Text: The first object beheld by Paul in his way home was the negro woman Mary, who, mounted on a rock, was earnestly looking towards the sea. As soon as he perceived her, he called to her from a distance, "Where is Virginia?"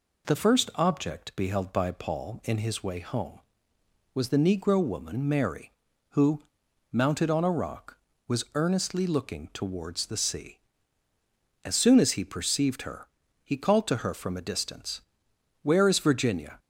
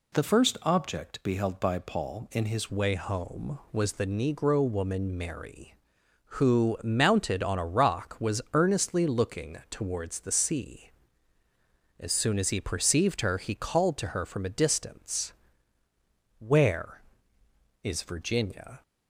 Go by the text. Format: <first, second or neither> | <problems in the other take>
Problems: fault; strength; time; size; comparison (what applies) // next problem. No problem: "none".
first | changes voice at "way"; from 2.6 s on; 16.2 s long